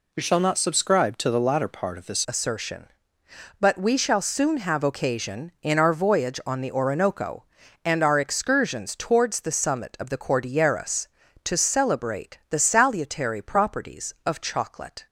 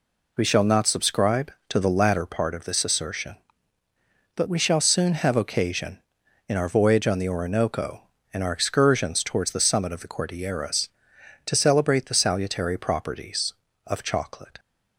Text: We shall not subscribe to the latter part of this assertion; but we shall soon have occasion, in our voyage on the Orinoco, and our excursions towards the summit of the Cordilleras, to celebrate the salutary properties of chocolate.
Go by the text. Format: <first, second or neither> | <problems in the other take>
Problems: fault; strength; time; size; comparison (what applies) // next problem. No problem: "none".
second | changes voice at "assertion"; from 2.2 s on; 12.8 s long